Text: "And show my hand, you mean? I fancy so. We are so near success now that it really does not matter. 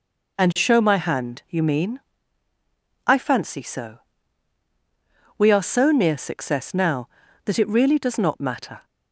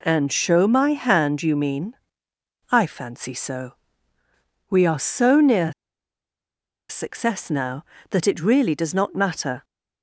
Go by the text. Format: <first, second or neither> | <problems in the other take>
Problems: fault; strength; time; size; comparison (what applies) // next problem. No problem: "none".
first | pauses between "near" and "success"; at 5.7 s; 1.1 s long